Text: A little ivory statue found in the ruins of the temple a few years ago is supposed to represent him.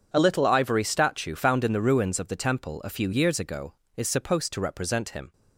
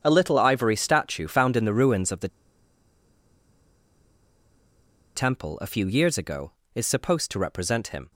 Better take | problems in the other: first | pauses between "the" and "temple"; strong; at 2.2 s; 2.8 s long

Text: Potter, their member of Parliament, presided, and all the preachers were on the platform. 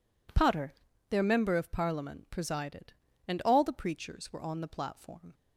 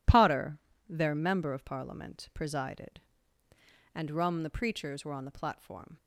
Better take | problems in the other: first | says "rum" for "all"; at 4.1 s

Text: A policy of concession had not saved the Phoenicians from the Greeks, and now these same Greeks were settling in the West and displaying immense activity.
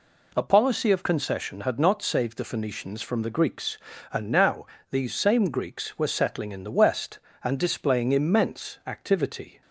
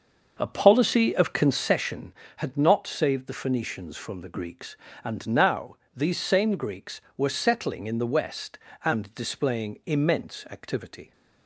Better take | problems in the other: first | starts louder than the rest; until 1.9 s; 6.5 dB // pauses between "now" and "these"; slight; at 5.7 s; 0.18 s long; slight in the first

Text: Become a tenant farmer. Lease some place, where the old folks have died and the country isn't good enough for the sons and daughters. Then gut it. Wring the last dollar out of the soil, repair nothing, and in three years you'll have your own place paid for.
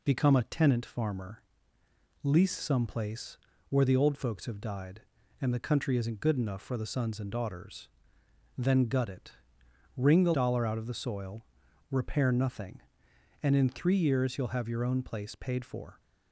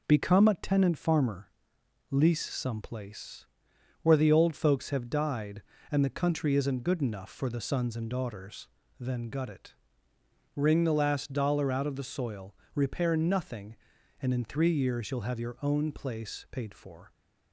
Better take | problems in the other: second | skips "last"; at 10.3 s

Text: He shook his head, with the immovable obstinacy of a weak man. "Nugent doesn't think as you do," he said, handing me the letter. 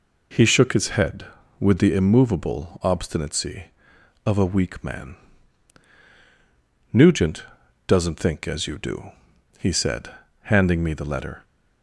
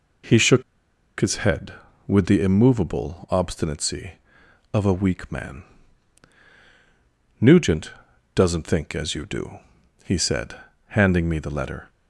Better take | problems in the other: first | pauses between "shook" and "his"; noticeable; at 0.6 s; 0.56 s long // pauses between "Nugent" and "doesn't"; at 7.9 s; 0.42 s long; also in the first

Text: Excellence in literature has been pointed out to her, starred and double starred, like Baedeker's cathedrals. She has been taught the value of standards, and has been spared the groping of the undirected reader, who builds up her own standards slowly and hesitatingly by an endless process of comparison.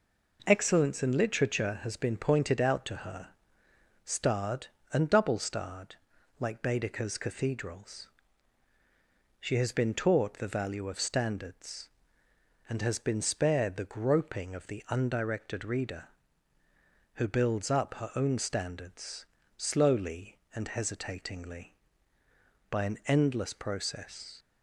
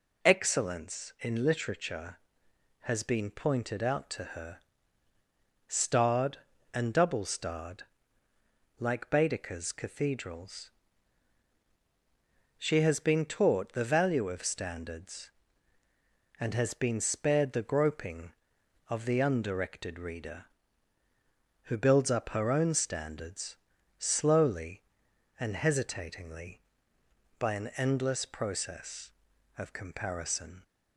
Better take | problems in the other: second | pauses between "standards" and "slowly"; slight; at 19.2 s; 0.30 s long; also in the second // stops before "of comparison"; at 24.3 s

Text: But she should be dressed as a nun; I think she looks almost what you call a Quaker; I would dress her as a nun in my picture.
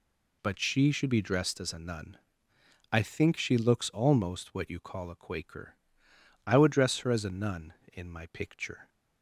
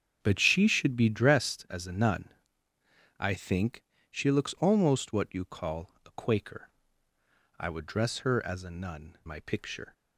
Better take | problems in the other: first | starts louder than the rest; strong; until 1.2 s; 7.5 dB // pauses between "think" and "she"; slight; at 3.8 s; 0.28 s long // skips "in"; at 9.2 s

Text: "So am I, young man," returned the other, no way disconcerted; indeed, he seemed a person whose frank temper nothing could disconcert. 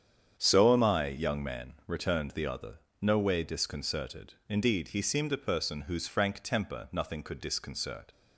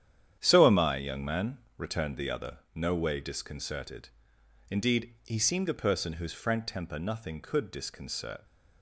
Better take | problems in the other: neither | starts louder than the rest; strong; the same in both

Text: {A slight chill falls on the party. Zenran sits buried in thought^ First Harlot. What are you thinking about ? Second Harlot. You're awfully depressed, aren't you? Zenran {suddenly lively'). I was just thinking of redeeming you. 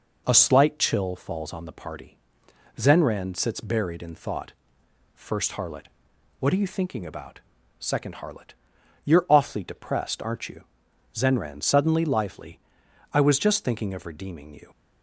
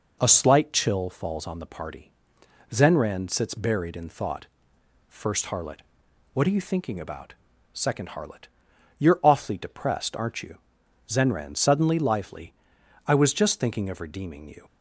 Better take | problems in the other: neither | pauses between "thought" and "First"; noticeable; the same in both

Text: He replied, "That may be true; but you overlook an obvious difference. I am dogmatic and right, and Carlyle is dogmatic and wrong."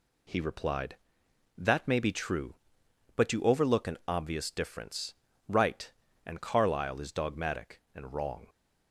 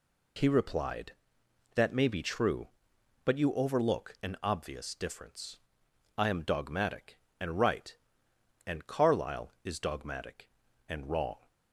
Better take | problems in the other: second | skips "I am dogmatic and"; at 5.3 s

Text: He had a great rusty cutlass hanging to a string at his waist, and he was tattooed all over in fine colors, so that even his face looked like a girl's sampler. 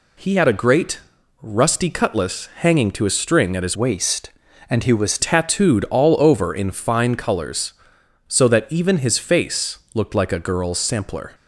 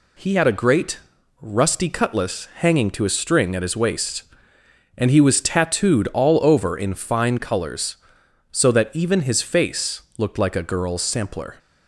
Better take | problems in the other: second | pauses between "great" and "rusty"; at 0.9 s; 0.44 s long; also in the second // changes voice from "waist" to "was"; from 3.7 to 5.1 s; 1.4 s long // pauses between "face" and "looked"; slight; at 9.7 s; 0.16 s long; slight in the second

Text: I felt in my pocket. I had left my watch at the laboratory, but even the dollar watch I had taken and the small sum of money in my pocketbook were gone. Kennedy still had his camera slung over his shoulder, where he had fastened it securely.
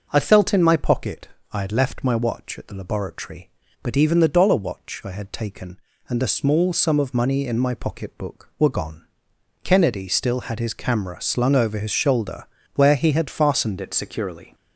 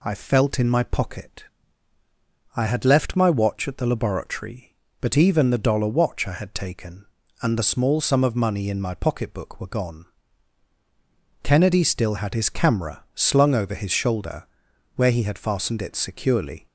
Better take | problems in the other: second | starts louder than the rest; until 1.1 s; 6.5 dB // changes voice at "it"; from 13.8 s on; 0.7 s long

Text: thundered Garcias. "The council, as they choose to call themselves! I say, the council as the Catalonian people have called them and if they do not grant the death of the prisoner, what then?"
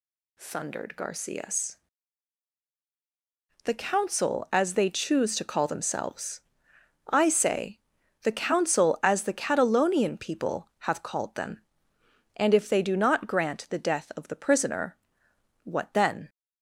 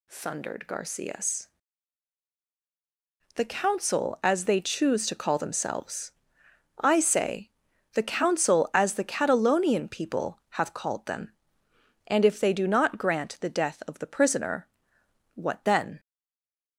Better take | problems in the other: first | stays silent after the last word; slight; from 15.9 s on; 0.8 s long

